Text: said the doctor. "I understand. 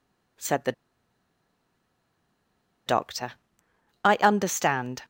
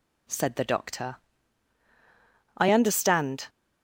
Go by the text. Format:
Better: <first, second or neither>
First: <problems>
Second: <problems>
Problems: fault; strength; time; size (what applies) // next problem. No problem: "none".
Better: second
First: pauses between "the" and "doctor"; strong; at 0.7 s; 2.1 s long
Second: none